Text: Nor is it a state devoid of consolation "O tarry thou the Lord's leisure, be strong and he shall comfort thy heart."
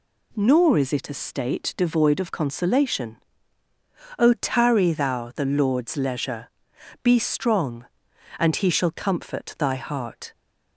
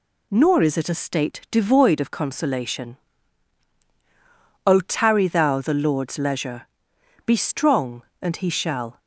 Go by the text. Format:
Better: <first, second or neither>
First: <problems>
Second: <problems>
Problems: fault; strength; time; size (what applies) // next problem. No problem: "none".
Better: first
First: pauses between "consolation" and "O"; at 3.1 s; 0.99 s long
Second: pauses between "consolation" and "O"; strong; at 2.9 s; 1.7 s long // stops before "comfort thy heart"; at 8.9 s